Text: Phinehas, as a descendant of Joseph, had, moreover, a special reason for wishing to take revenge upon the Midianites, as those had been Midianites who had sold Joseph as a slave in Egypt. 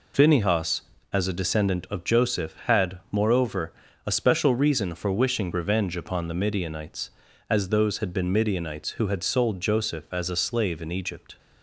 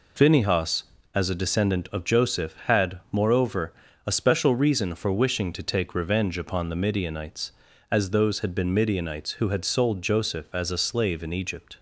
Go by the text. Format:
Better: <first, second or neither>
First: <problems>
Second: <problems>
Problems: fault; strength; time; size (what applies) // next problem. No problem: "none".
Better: second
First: skips "to take"; at 5.5 s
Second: none